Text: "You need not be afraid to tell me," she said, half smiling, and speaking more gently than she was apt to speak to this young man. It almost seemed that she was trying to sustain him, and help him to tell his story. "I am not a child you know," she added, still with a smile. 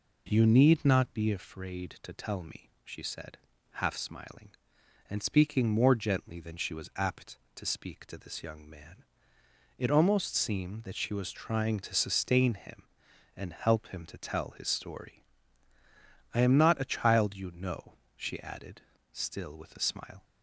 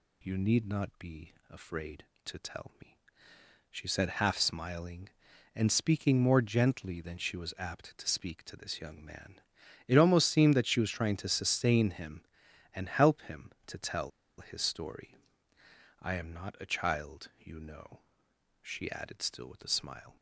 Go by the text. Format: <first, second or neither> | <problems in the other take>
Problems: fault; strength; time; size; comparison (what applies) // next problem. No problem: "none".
first | pauses between "be" and "afraid"; slight; at 1.3 s; 0.18 s long // pauses between "tell" and "his"; slight; at 14.1 s; 0.29 s long